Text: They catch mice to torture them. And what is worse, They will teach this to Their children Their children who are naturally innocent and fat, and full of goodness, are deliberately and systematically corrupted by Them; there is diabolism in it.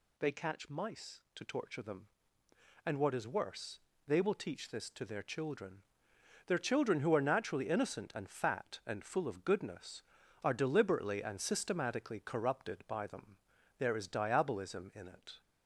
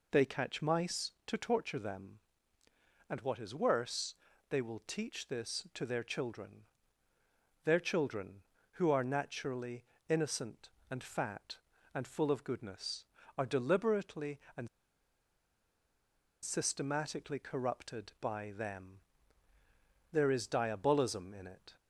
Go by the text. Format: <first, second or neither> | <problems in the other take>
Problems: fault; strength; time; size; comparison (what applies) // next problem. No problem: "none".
first | pauses between "children" and "Their"; at 6.6 s; 1.0 s long; noticeable in the first // pauses between "naturally" and "innocent"; slight; at 9.8 s; 0.22 s long // pauses between "and" and "systematically"; strong; at 14.6 s; 1.7 s long